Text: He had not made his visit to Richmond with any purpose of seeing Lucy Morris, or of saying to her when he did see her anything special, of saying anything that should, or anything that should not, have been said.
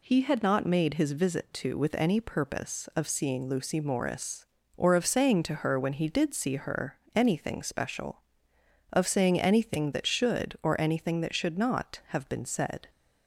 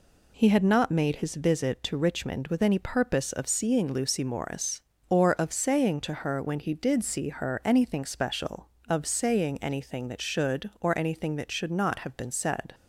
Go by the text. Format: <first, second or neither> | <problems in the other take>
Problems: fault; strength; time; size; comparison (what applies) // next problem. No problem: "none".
second | skips "Richmond"; at 1.7 s // pauses between "her" and "anything"; slight; at 6.9 s; 0.16 s long